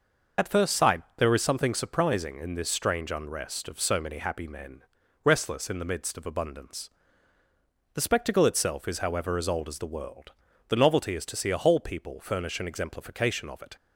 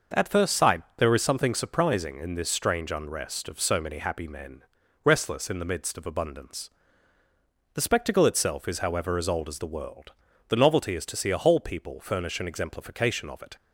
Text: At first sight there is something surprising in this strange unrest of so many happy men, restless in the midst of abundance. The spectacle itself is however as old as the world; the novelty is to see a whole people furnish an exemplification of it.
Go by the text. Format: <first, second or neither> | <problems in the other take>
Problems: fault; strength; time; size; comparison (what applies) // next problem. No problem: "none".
second | loses the start of "At"; at 0.3 s; 75 ms // pauses between "sight" and "there"; slight; at 1.0 s; 0.16 s long; slight in the second